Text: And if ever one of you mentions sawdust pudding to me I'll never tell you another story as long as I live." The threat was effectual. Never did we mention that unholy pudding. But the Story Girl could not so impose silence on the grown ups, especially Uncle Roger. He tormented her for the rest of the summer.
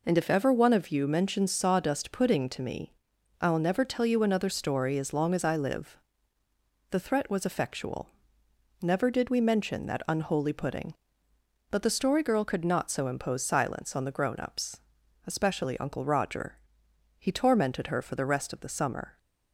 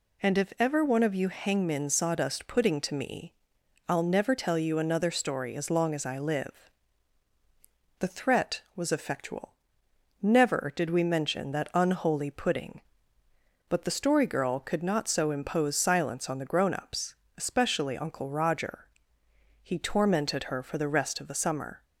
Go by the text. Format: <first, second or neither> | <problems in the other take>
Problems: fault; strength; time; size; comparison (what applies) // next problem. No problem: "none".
first | says "hangmen" for "mentions"; at 1.2 s // pauses between "me" and "I'll"; noticeable; at 3.3 s; 0.58 s long; noticeable in the first